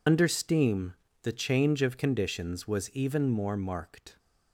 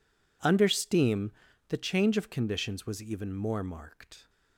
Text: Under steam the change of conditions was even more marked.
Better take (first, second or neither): second